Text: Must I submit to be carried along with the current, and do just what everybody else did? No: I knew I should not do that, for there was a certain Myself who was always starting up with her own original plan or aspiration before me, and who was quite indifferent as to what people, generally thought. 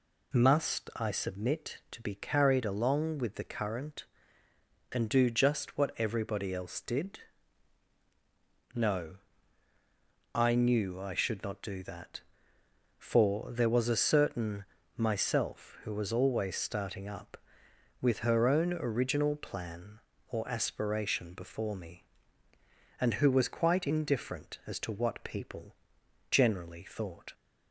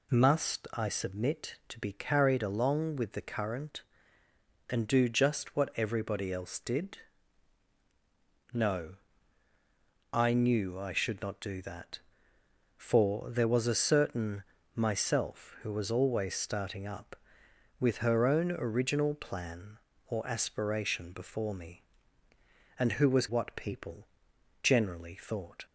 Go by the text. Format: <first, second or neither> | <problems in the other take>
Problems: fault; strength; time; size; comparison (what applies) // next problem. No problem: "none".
first | pauses between "certain" and "Myself"; slight; at 14.4 s; 0.32 s long; slight in the first // skips "quite indifferent as to"; at 23.2 s